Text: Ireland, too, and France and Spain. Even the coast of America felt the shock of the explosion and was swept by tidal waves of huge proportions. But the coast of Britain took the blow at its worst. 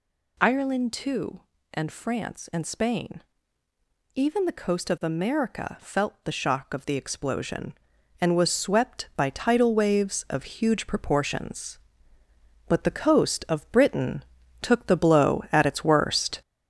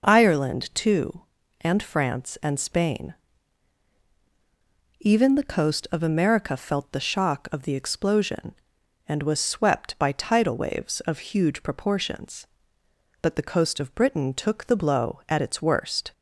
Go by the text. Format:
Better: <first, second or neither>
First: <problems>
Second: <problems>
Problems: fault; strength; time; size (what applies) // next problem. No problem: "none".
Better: second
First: gets louder; noticeable; throughout; 4.5 dB // pauses between "Britain" and "took"; at 14.2 s; 0.40 s long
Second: none